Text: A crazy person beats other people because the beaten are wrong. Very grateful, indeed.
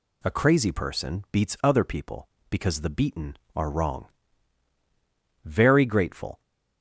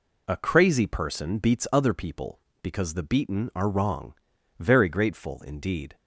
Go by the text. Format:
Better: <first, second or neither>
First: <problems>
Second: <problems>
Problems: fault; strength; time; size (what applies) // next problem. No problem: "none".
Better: second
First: stops before "indeed"; at 6.4 s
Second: none